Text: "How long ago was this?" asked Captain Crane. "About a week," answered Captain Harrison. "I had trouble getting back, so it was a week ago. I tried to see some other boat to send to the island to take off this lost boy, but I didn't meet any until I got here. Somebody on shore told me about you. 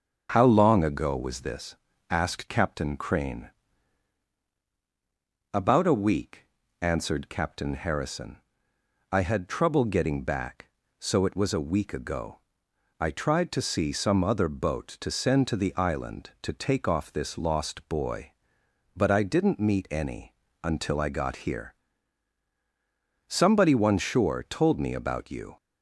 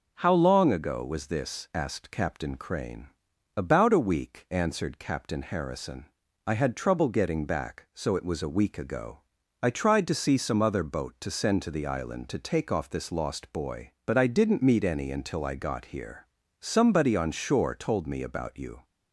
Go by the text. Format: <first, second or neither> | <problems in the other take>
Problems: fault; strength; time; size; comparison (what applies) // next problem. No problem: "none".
second | starts louder than the rest; until 1.3 s; 6.5 dB; noticeable in the second // pauses between "any" and "until"; slight; at 20.3 s; 0.30 s long // says "one" for "on"; at 23.7 s